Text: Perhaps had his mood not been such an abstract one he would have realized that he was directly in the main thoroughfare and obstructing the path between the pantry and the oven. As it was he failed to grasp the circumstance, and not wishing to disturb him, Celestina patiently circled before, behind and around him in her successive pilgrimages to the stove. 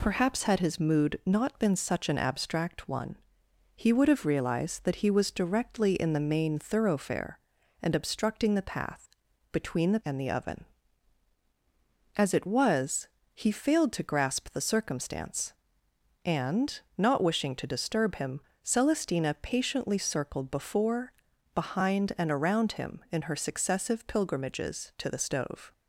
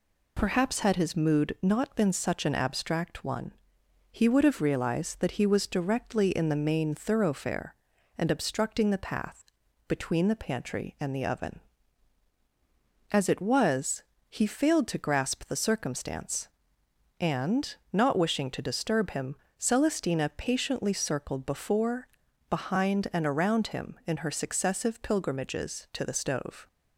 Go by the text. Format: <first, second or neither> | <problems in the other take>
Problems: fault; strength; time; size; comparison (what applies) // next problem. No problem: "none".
second | pauses between "one" and "he"; noticeable; at 3.1 s; 0.58 s long; noticeable in the second // pauses between "path" and "between"; at 9.0 s; 0.42 s long; also in the second // skips "pantry"; at 10.0 s // pauses between "was" and "he"; slight; at 13.0 s; 0.26 s long; slight in the second // pauses between "and" and "not"; slight; at 16.7 s; 0.16 s long; slight in the second